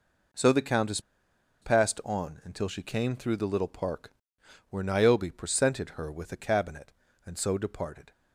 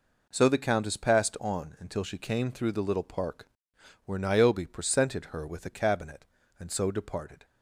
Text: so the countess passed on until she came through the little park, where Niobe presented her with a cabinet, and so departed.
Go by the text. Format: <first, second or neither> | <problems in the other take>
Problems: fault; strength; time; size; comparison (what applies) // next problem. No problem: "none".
second | pauses between "countess" and "passed"; noticeable; at 0.9 s; 0.62 s long